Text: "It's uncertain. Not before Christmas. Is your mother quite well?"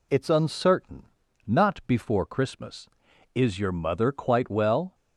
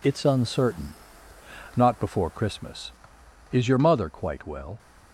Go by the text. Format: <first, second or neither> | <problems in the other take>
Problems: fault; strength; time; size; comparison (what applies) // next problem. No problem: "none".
neither | none